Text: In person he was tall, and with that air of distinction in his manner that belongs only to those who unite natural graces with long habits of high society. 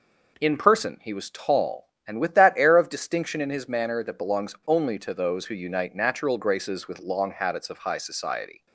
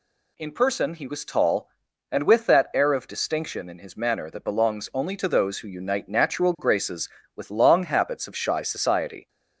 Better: first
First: none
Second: says "shy" for "high"; at 8.3 s

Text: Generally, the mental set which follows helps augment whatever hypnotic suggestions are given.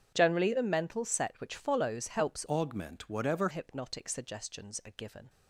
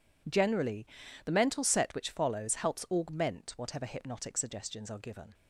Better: second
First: starts louder than the rest; strong; until 1.1 s; 8.5 dB // changes voice from "augment" to "whatever"; from 2.4 to 3.4 s; 1.0 s long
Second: none

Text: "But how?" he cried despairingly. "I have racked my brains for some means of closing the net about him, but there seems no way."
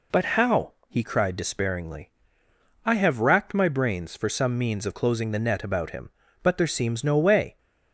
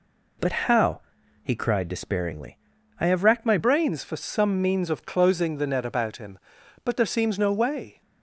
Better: first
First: none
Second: changes voice at "brains"; from 3.5 s on; 4.5 s long

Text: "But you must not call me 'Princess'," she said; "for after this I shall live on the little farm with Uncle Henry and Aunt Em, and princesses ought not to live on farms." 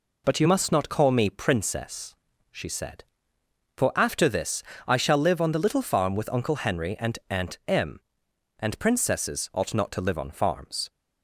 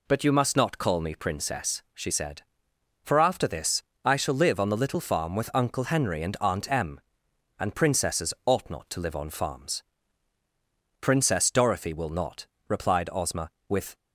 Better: first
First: pauses between "this" and "I"; slight; at 4.6 s; 0.24 s long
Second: pauses between "this" and "I"; slight; at 3.8 s; 0.22 s long // goes on to say "Princess Dorothy will not replied Ozma with"; strong; from 11.0 s on; 2.9 s long

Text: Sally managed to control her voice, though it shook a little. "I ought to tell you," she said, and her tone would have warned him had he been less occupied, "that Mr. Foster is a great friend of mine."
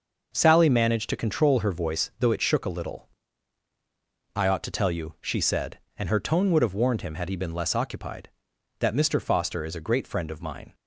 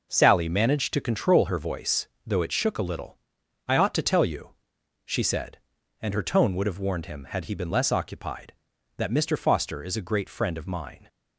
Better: neither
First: none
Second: none

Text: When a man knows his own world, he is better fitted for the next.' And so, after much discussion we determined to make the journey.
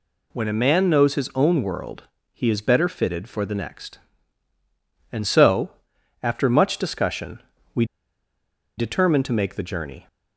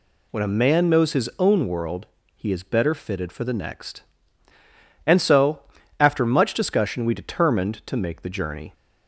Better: second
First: pauses between "discussion" and "we"; slight; at 7.4 s; 0.34 s long // pauses between "we" and "determined"; noticeable; at 7.8 s; 0.93 s long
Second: none

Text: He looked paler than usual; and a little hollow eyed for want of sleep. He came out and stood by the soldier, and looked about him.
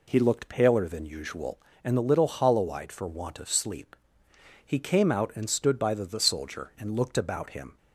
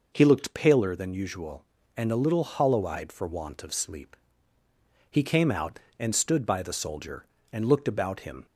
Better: second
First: says "the" twice; at 6.0 s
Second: none

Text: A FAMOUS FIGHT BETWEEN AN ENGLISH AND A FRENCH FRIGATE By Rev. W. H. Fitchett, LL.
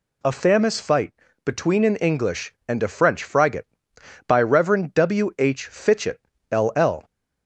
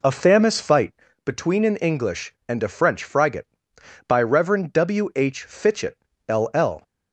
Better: first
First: pauses between "FIGHT" and "BETWEEN"; slight; at 1.1 s; 0.32 s long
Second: starts louder than the rest; slight; until 1.2 s; 3.5 dB // pauses between "FIGHT" and "BETWEEN"; slight; at 0.9 s; 0.32 s long

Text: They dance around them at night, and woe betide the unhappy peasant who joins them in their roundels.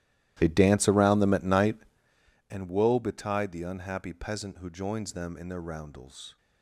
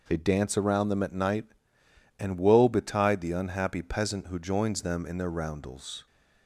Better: second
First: starts louder than the rest; strong; until 2.2 s; 14.5 dB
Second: none

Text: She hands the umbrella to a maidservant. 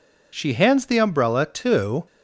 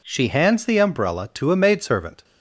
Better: second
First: stops before "a maidservant"; at 2.0 s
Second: none

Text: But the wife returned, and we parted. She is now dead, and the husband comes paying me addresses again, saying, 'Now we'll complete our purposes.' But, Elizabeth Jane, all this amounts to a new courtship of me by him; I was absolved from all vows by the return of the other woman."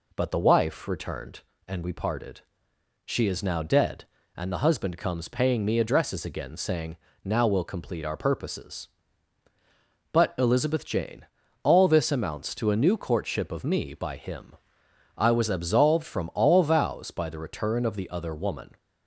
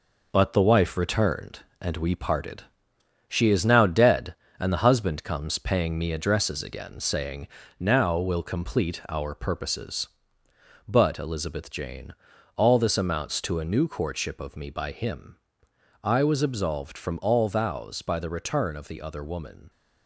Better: first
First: none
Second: gets quieter; noticeable; throughout; 6 dB

